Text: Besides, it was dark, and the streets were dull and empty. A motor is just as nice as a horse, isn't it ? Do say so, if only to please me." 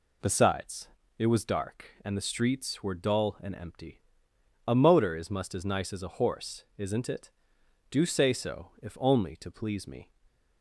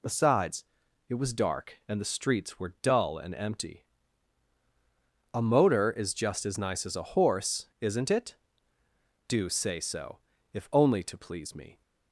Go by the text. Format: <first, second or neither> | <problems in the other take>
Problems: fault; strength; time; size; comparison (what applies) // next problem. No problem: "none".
second | says "must" for "just"; at 5.3 s